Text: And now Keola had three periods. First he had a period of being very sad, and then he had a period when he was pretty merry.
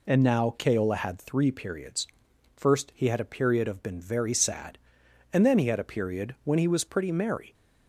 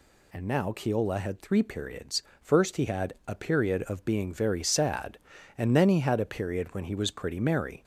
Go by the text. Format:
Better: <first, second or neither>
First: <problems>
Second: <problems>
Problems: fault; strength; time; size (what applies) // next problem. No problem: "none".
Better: second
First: says "been" for "being"; at 3.8 s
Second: none